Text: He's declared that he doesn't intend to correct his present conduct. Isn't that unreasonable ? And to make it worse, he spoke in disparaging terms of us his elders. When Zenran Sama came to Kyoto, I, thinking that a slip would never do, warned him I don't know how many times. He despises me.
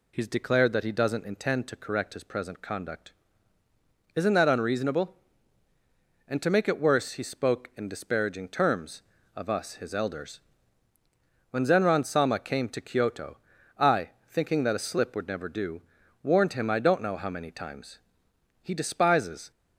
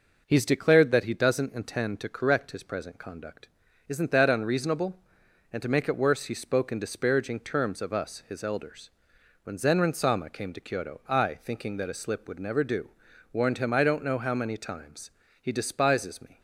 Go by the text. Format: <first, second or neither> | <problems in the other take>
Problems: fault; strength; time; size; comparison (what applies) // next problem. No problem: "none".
second | stops before "me"; at 19.5 s